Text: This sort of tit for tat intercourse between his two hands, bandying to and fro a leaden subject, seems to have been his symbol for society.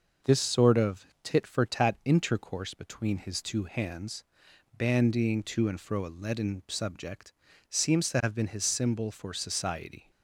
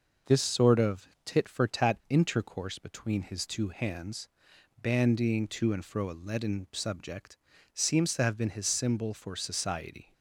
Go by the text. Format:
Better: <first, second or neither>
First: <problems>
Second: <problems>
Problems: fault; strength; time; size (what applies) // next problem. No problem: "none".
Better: neither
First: pauses between "of" and "tit"; slight; at 1.0 s; 0.18 s long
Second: pauses between "of" and "tit"; slight; at 1.0 s; 0.18 s long